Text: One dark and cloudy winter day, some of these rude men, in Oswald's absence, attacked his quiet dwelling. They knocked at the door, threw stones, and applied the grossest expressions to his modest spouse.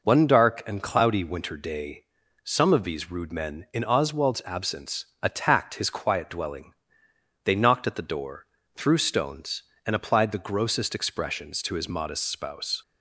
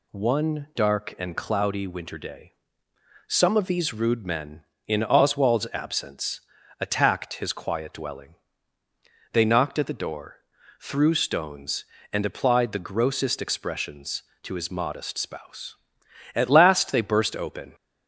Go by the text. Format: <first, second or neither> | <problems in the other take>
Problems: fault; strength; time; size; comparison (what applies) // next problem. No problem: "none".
first | goes on to say "At last they burst open"; from 16.3 s on; 1.4 s long